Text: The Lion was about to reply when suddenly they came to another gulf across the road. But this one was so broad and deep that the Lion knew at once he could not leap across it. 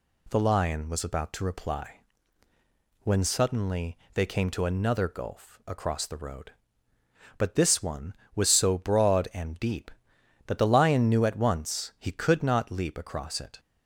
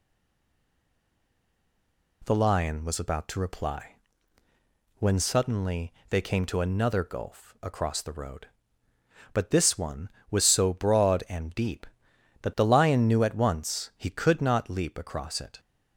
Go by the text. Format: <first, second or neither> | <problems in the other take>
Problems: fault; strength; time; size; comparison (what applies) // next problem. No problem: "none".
first | stays silent before the first word; until 2.2 s; 2.2 s long // pauses between "reply" and "when"; at 3.9 s; 1.0 s long; also in the first // pauses between "suddenly" and "they"; slight; at 5.9 s; 0.18 s long; slight in the first